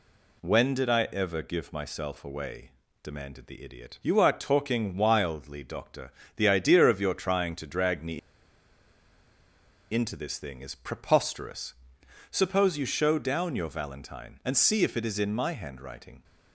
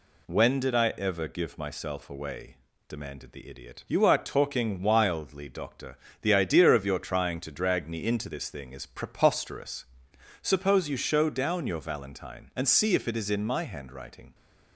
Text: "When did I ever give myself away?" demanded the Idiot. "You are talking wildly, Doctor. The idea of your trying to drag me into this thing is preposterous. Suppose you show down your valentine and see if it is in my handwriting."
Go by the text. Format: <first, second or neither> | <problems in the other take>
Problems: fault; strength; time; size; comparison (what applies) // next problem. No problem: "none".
second | pauses between "me" and "into"; strong; at 8.1 s; 1.7 s long